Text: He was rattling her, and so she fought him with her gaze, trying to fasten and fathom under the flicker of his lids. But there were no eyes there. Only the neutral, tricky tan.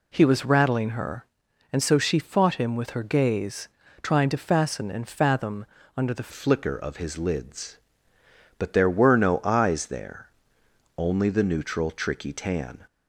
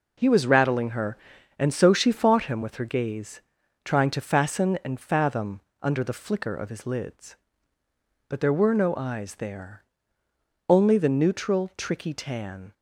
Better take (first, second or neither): second